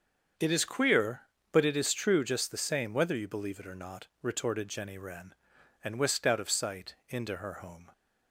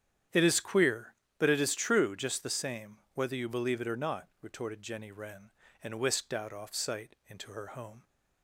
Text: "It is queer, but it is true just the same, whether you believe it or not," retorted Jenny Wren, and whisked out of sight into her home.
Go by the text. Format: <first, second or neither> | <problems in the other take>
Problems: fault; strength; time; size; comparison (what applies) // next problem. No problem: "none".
first | starts louder than the rest; strong; until 1.5 s; 9.5 dB; also in the first // says "off" for "of"; at 6.5 s